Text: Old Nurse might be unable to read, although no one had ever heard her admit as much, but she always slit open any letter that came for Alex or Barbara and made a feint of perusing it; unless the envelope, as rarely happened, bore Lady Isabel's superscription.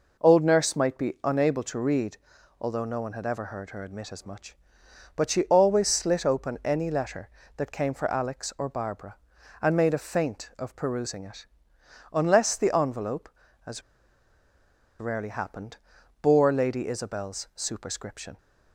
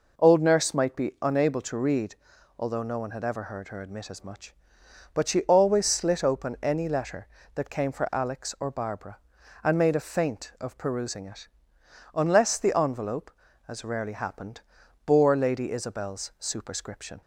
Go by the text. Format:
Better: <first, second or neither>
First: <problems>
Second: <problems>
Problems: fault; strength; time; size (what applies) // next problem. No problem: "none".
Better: second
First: pauses between "as" and "rarely"; at 13.8 s; 1.1 s long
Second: none